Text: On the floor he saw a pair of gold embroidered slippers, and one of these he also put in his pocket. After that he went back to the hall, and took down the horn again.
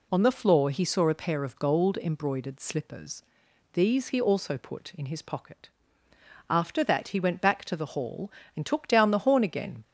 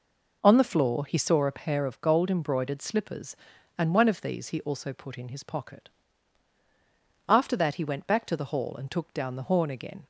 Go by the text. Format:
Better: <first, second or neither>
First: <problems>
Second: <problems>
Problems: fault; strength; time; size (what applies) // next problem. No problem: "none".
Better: second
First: skips "and one of"; at 3.4 s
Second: none